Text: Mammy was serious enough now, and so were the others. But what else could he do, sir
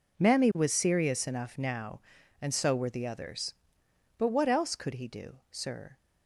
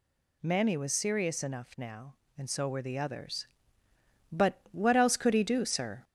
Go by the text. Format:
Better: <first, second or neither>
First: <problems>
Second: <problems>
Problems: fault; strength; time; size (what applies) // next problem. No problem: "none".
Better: first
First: none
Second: gets louder; slight; throughout; 2 dB